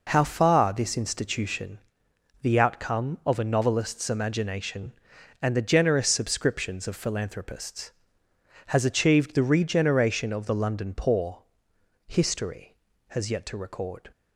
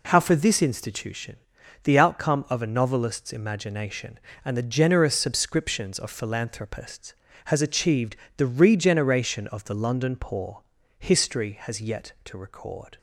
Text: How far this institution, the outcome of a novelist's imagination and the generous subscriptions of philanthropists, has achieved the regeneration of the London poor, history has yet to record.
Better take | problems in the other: first | says "for" for "far"; at 0.1 s // pauses between "achieved" and "the"; slight; at 8.1 s; 0.22 s long

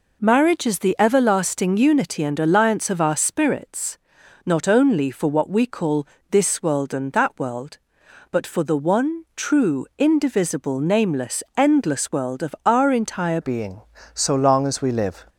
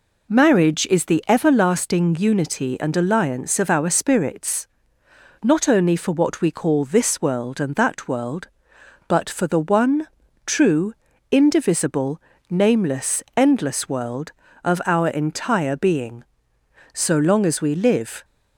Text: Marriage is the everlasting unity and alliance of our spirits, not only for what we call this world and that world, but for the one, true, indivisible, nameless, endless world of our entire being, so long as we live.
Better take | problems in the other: second | pauses between "call" and "this"; slight; at 6.0 s; 0.26 s long // changes voice at "being"; from 13.4 s on; 1.8 s long

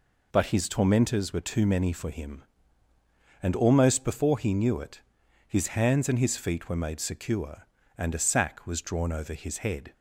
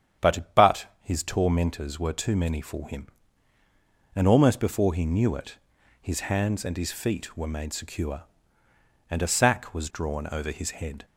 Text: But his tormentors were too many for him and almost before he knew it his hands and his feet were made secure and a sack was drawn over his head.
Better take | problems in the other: first | starts louder than the rest; strong; until 1.3 s; 8.5 dB // says "But" twice; at 0.5 s // pauses between "it" and "his"; at 5.5 s; 0.42 s long; noticeable in the first

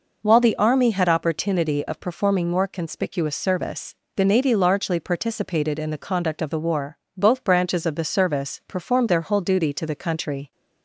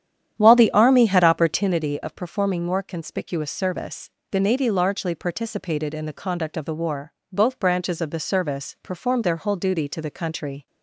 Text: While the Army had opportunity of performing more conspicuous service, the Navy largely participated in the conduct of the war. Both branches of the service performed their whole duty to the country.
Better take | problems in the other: first | starts louder than the rest; strong; until 1.8 s; 10 dB

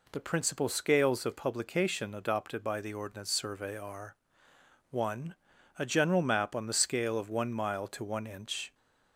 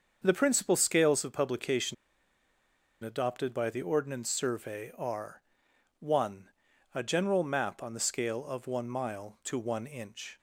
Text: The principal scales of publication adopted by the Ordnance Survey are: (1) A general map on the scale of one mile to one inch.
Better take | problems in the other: first | starts louder than the rest; until 1.2 s; 6.5 dB // pauses between "publication" and "adopted"; at 1.9 s; 1.0 s long

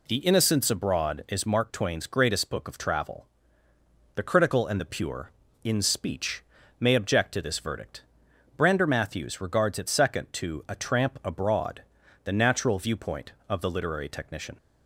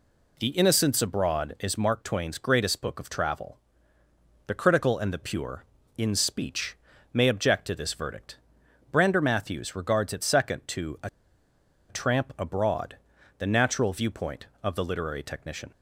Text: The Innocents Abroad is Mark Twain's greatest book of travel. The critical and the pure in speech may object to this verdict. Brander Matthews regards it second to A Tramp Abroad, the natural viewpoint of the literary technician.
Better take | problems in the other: first | pauses between "speech" and "may"; at 6.7 s; 0.38 s long; also in the first // pauses between "A" and "Tramp"; noticeable; at 11.0 s; 0.80 s long

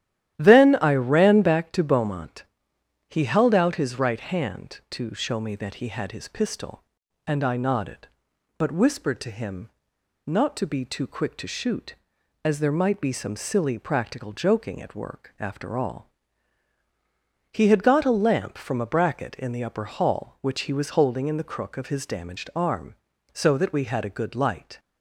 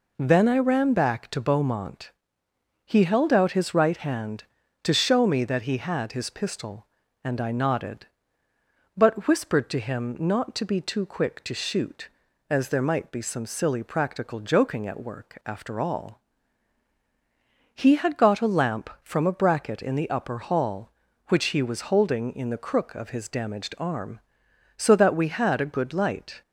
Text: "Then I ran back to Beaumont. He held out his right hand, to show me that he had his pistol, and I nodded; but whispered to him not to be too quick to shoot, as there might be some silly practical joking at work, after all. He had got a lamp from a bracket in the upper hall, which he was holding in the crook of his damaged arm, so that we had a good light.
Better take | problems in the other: second | starts louder than the rest; strong; until 1.3 s; 12.5 dB // pauses between "him" and "not"; noticeable; at 9.6 s; 0.56 s long

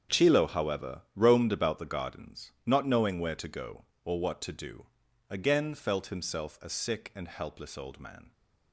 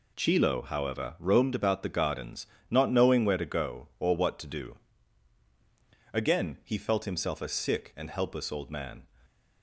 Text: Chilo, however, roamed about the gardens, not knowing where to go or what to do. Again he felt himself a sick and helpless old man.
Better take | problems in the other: second | starts louder than the rest; strong; until 1.2 s; 7.5 dB // skips "he"; at 5.7 s

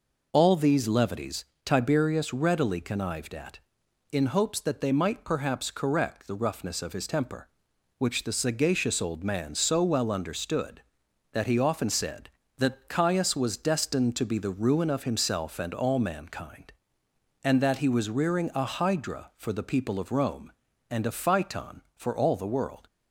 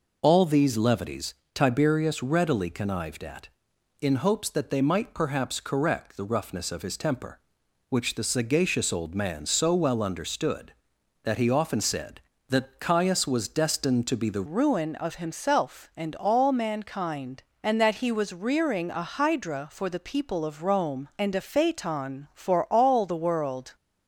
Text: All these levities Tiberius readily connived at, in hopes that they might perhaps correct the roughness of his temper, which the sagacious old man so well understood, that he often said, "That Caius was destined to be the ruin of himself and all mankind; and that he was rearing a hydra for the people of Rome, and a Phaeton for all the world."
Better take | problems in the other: first | pauses between "levities" and "Tiberius"; slight; at 1.3 s; 0.20 s long; slight in the first // changes voice at "ruin"; from 14.4 s on; 9.3 s long

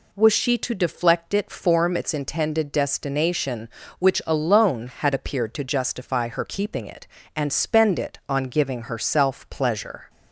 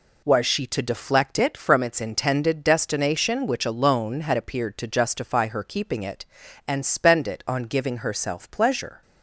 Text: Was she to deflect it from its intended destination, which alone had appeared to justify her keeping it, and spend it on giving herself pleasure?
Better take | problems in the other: second | says "form" for "from"; at 1.4 s

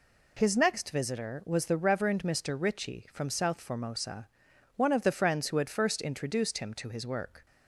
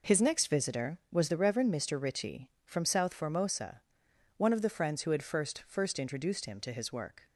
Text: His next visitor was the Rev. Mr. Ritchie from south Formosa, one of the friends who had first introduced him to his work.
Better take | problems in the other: first | says "first" twice; at 5.6 s

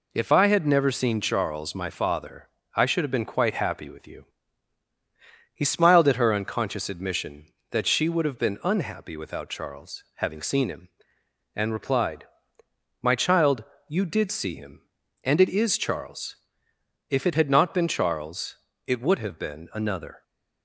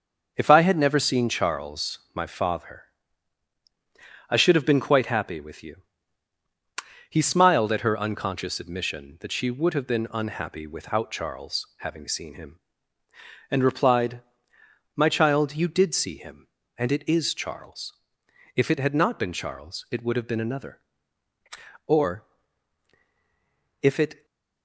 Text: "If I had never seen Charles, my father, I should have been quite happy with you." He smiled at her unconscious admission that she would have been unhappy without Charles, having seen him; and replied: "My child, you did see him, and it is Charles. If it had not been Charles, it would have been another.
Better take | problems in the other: first | starts louder than the rest; until 1.3 s; 6.5 dB // goes on to say "Or if it"; strong; from 21.8 s on; 2.3 s long // stays silent after the last word; slight; from 24.1 s on; 0.5 s long

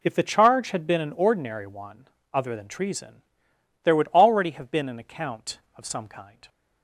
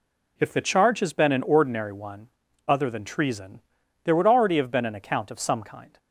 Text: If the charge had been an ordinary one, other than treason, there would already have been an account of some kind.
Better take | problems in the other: first | says "has" for "had"; at 0.9 s

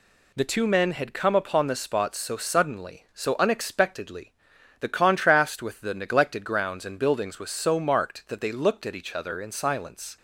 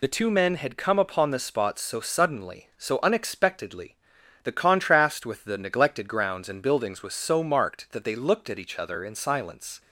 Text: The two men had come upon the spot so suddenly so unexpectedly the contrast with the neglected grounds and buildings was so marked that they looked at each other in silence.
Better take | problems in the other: first | loses the start of "The"; at 0.0 s; 45 ms // pauses between "unexpectedly" and "the"; noticeable; at 3.9 s; 0.48 s long; noticeable in the first

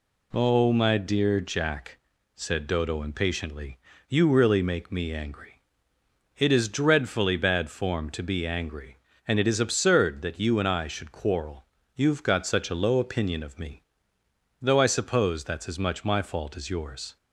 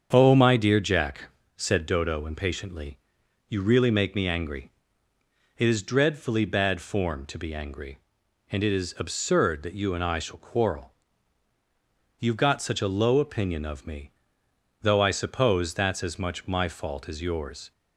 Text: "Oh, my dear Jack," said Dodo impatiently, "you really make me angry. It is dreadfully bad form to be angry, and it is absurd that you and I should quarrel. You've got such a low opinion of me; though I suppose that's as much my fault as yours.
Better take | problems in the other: first | starts louder than the rest; strong; until 1.1 s; 7 dB // says "shall" for "should"; at 10.1 s

